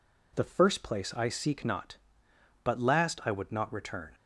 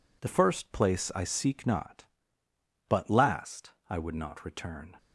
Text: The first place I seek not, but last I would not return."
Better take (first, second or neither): first